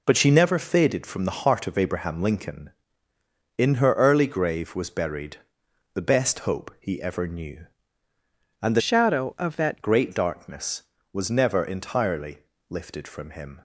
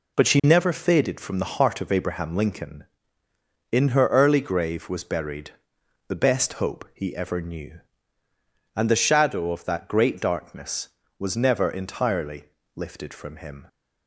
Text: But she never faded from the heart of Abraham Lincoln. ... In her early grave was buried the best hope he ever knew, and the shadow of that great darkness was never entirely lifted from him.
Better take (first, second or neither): second